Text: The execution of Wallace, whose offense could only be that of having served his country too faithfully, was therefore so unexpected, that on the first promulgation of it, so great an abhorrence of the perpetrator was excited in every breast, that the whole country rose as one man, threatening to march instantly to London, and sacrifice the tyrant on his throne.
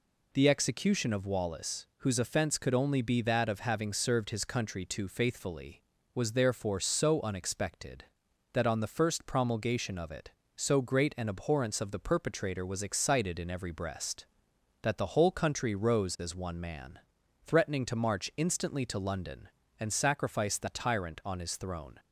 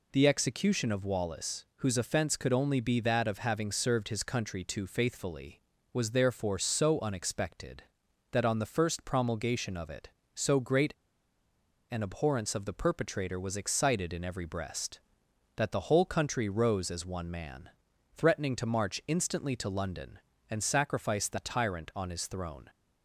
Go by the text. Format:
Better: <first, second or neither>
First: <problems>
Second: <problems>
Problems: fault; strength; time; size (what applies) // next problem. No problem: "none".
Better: first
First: none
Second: pauses between "great" and "an"; noticeable; at 10.9 s; 0.97 s long